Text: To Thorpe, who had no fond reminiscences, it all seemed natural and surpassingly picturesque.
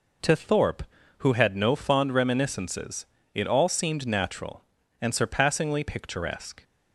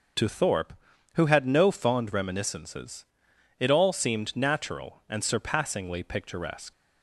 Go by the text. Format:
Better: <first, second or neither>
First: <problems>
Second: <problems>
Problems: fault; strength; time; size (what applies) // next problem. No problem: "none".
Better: first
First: none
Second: starts louder than the rest; noticeable; until 1.5 s; 6 dB // leaves "picturesque" unfinished; at 6.7 s; 75 ms